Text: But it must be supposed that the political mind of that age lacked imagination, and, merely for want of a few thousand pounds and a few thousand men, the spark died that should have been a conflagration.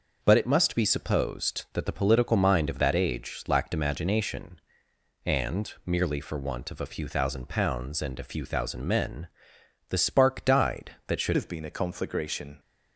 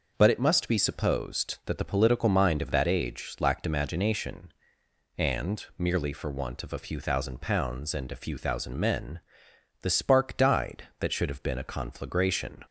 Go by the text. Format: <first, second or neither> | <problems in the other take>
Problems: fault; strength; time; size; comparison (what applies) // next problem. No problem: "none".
second | changes voice at "have"; from 11.3 s on; 1.2 s long